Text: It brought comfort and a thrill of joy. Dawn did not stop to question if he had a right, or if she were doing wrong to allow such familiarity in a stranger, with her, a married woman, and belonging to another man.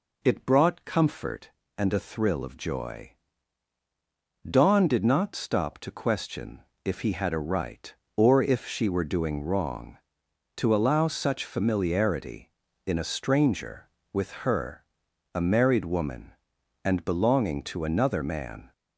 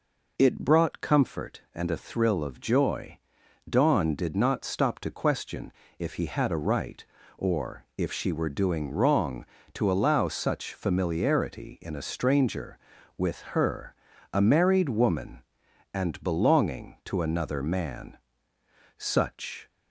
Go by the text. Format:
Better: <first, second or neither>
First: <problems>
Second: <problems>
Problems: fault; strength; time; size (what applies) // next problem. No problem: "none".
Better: first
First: pauses between "question" and "if"; slight; at 6.5 s; 0.24 s long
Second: pauses between "question" and "if"; slight; at 5.7 s; 0.26 s long // goes on to say "Such"; noticeable; from 18.9 s on; 0.70 s long